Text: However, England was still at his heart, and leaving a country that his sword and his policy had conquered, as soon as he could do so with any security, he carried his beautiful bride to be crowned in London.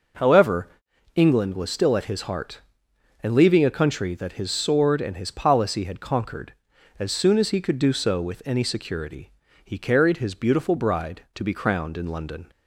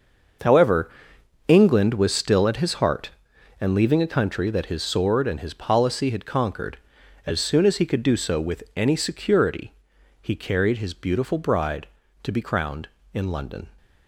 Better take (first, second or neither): first